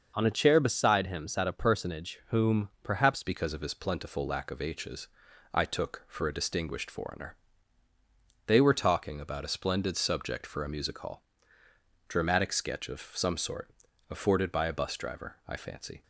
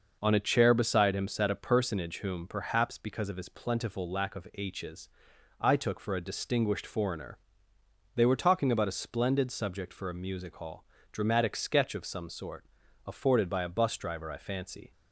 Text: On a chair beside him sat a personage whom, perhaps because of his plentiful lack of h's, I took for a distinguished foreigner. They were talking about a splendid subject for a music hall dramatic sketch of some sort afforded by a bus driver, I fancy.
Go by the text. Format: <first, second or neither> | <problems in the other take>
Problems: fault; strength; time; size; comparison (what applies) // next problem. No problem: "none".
second | starts louder than the rest; noticeable; until 1.1 s; 6 dB // changes voice at "because"; from 3.2 s on; 12.8 s long // pauses between "hall" and "dramatic"; noticeable; at 11.2 s; 0.86 s long; slight in the second // pauses between "sort" and "afforded"; at 13.6 s; 0.40 s long; also in the second